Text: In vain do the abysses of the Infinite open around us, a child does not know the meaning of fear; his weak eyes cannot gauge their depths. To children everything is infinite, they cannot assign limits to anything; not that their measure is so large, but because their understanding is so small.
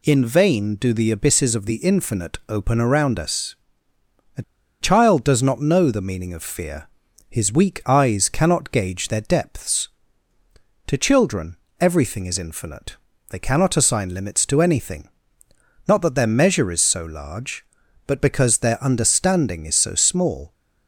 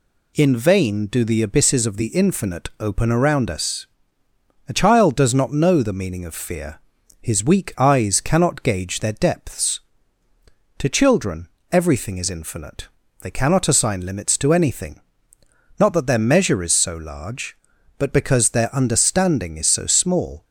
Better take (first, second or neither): second